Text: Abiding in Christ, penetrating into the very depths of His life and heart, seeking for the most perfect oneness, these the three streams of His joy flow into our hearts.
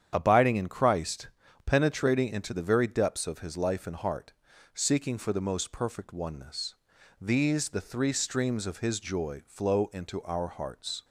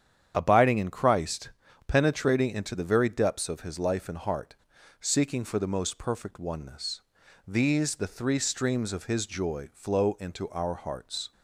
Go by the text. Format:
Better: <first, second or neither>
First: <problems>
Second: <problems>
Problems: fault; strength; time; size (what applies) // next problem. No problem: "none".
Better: neither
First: starts louder than the rest; strong; until 1.1 s; 9 dB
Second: starts louder than the rest; strong; until 1.3 s; 9 dB